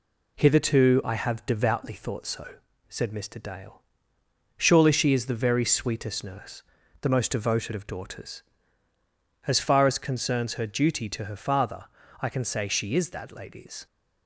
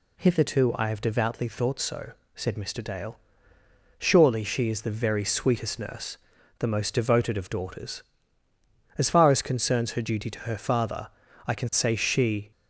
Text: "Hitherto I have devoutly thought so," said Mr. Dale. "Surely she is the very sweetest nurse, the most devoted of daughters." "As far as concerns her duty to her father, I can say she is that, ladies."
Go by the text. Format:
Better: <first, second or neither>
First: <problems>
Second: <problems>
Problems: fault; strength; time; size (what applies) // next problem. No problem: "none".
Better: first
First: none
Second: stops before "is that ladies"; at 12.5 s